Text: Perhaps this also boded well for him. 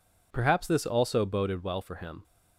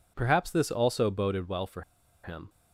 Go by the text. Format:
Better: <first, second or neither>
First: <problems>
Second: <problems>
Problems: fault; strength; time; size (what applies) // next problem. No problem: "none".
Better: first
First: none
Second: pauses between "for" and "him"; at 1.8 s; 0.42 s long